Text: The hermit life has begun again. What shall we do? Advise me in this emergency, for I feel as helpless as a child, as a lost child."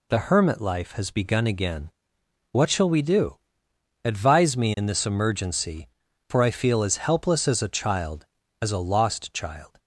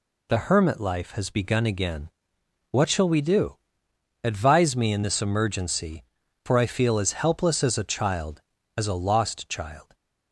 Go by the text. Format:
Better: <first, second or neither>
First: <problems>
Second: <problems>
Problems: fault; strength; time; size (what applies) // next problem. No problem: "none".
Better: neither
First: none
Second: none